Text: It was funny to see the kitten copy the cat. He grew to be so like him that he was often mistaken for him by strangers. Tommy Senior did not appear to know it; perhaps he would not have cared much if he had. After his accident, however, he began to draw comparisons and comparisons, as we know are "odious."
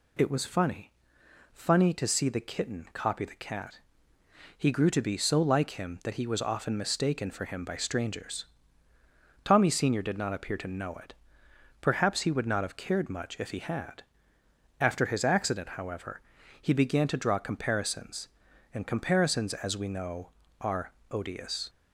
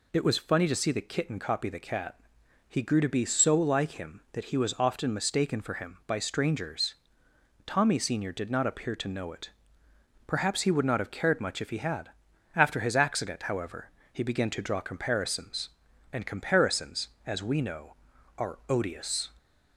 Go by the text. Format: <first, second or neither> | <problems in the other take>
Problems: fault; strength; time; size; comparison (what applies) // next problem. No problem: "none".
second | says "funny" twice; at 1.5 s // pauses between "are" and "odious"; slight; at 20.9 s; 0.20 s long